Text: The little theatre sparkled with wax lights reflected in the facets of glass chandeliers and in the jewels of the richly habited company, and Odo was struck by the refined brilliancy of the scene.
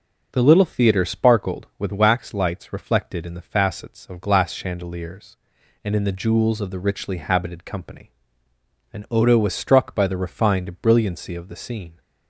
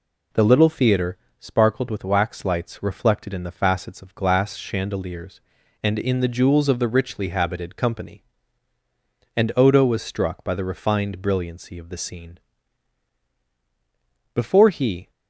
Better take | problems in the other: first | pauses between "theatre" and "sparkled"; slight; at 1.1 s; 0.22 s long // goes on to say "Before he"; noticeable; from 14.3 s on; 0.76 s long

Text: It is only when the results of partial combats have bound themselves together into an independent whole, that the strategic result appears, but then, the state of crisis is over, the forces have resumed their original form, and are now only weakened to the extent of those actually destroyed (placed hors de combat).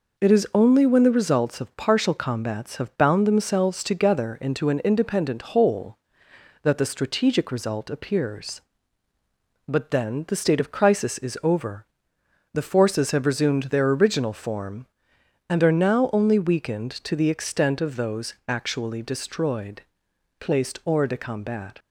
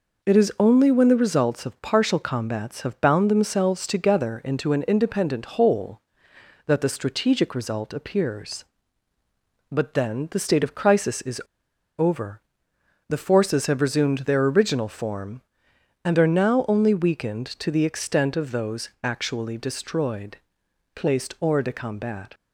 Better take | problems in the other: first | pauses between "is" and "over"; noticeable; at 11.3 s; 0.58 s long // pauses between "those" and "actually"; slight; at 18.8 s; 0.16 s long; slight in the first

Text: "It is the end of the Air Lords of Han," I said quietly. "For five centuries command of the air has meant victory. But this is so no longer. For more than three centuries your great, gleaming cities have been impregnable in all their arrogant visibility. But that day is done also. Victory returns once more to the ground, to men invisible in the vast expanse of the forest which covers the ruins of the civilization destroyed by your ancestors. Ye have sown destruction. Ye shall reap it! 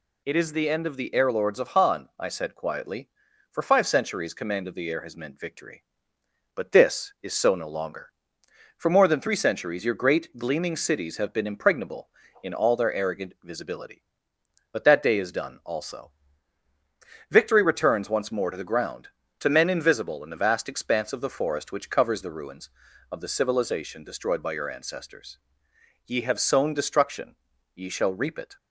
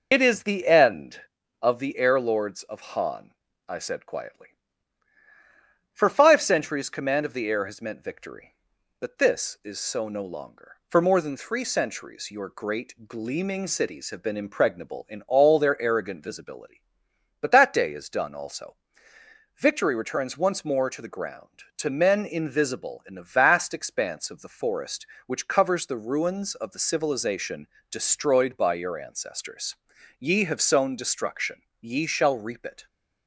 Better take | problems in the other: first | loses the start of "It"; at 0.1 s; 95 ms // pauses between "civilization" and "destroyed"; slight; at 27.6 s; 0.24 s long

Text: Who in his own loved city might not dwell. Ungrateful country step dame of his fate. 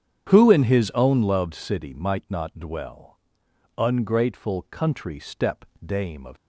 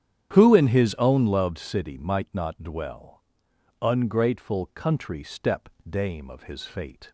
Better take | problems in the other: second | starts louder than the rest; strong; until 1.3 s; 9 dB; strong in the second // pauses between "step" and "dame"; slight; at 5.6 s; 0.22 s long; slight in the second // stops before "his fate"; at 6.3 s

